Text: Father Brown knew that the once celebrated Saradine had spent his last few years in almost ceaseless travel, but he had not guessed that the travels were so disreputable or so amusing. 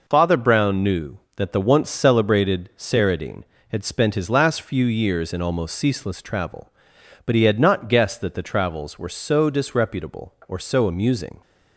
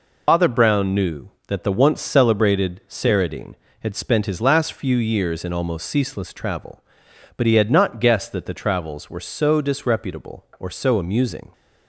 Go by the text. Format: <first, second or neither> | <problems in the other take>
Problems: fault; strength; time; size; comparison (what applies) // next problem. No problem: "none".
first | loses the start of "Father"; at 0.2 s; 80 ms